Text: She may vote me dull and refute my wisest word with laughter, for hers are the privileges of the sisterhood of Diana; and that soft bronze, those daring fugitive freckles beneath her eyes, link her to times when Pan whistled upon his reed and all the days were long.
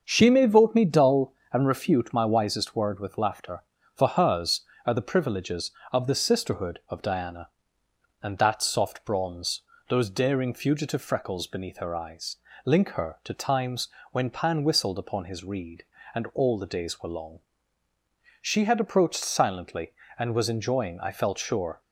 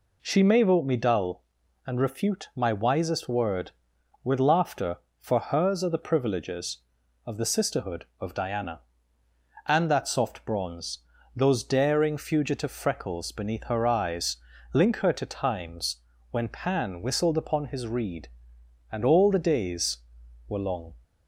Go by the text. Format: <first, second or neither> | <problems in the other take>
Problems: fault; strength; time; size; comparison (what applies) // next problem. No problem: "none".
second | starts louder than the rest; until 1.0 s; 6.5 dB // pauses between "times" and "when"; slight; at 13.8 s; 0.22 s long; slight in the second // goes on to say "She had approached silently and was enjoying I felt sure"; strong; from 18.4 s on; 3.3 s long